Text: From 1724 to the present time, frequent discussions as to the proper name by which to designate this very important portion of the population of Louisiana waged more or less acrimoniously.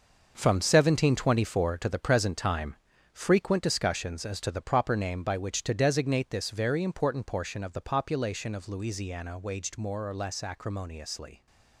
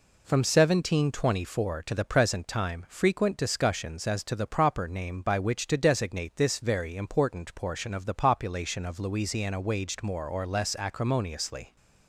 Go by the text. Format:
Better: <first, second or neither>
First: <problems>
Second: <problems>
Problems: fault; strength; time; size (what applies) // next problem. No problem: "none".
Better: second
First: gets quieter; strong; throughout; 10.5 dB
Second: none